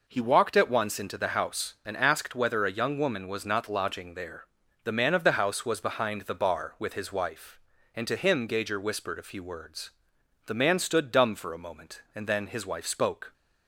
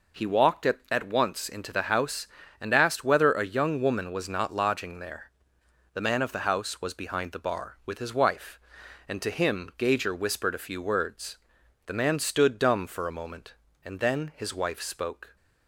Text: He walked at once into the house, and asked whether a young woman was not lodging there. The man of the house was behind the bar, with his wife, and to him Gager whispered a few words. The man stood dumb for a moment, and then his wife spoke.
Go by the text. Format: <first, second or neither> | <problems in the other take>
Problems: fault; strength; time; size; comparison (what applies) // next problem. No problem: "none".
first | says "at" twice; at 0.8 s